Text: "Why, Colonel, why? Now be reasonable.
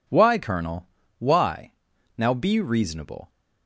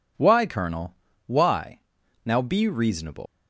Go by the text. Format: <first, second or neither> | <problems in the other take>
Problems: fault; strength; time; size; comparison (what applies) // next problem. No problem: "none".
first | leaves "reasonable" unfinished; at 3.2 s; 110 ms